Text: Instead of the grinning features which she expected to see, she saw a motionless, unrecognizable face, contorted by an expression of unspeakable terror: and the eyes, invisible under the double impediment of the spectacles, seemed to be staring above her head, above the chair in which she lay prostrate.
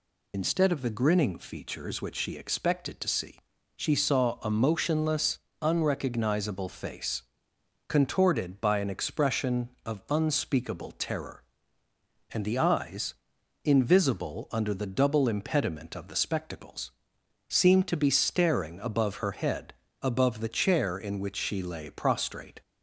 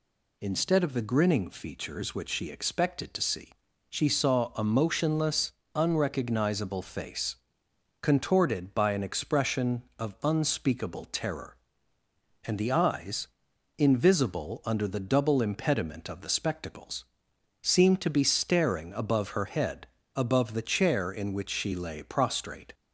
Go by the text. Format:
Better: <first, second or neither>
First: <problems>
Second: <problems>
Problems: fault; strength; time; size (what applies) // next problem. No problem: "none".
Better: second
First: loses the start of "Instead"; at 0.3 s; 55 ms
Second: none